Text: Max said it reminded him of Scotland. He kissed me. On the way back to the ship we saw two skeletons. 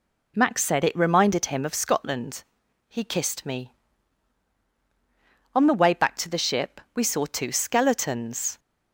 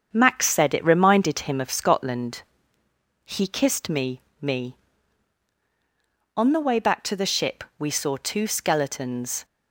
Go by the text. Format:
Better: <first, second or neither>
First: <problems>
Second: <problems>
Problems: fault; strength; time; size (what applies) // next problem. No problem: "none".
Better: first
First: none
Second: starts louder than the rest; strong; until 1.1 s; 7.5 dB // says "me" twice; at 4.4 s